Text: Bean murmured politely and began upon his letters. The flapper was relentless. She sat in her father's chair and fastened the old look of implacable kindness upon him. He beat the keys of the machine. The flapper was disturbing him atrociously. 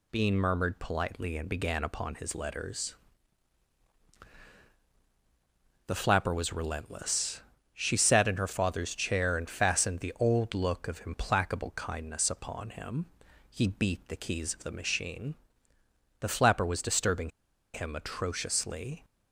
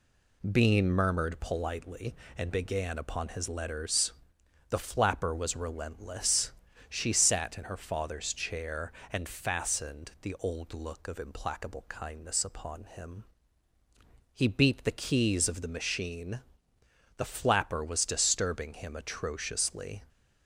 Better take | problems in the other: second | pauses between "disturbing" and "him"; at 17.2 s; 0.44 s long

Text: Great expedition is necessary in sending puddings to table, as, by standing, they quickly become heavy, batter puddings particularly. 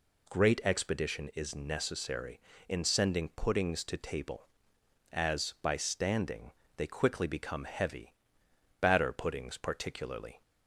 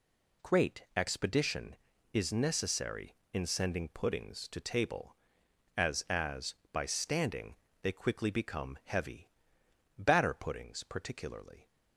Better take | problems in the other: first | says "as" twice; at 6.0 s

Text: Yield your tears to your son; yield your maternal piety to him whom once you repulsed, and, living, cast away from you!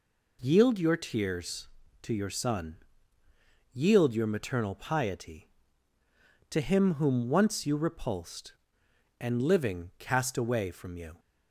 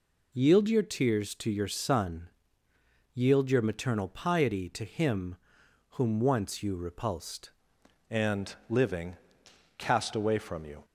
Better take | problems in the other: first | pauses between "him" and "whom"; noticeable; at 5.3 s; 0.56 s long // changes voice at "and"; from 8.0 s on; 2.8 s long

